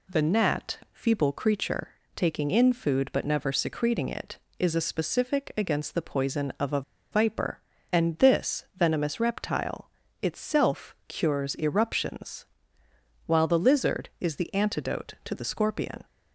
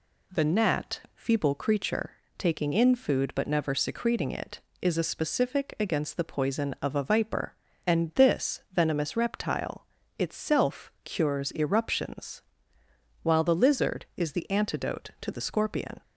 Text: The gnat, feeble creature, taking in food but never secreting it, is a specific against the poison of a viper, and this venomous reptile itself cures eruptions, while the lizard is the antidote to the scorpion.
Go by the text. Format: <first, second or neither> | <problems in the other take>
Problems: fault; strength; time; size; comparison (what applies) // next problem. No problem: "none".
second | pauses between "a" and "viper"; slight; at 6.8 s; 0.31 s long // pauses between "reptile" and "itself"; slight; at 9.8 s; 0.32 s long; slight in the second